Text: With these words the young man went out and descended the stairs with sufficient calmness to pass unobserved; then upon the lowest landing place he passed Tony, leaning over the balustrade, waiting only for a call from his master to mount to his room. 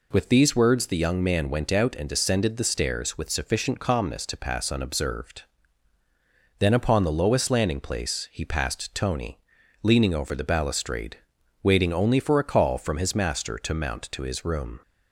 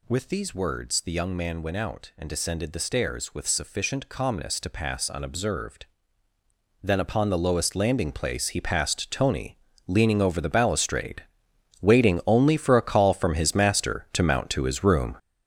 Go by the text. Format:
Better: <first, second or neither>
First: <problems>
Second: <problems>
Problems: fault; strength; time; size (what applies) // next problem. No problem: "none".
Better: first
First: none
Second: gets louder; strong; throughout; 9 dB